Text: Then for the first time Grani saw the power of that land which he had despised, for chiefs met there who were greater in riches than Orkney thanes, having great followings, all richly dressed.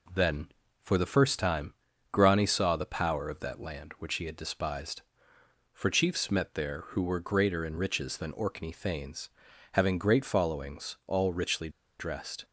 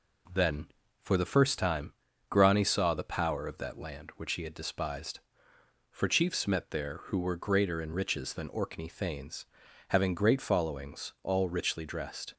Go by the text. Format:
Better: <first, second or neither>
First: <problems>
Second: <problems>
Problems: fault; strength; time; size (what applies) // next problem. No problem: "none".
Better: second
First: pauses between "time" and "Grani"; at 1.7 s; 0.38 s long // pauses between "richly" and "dressed"; slight; at 11.6 s; 0.30 s long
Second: pauses between "time" and "Grani"; at 1.9 s; 0.36 s long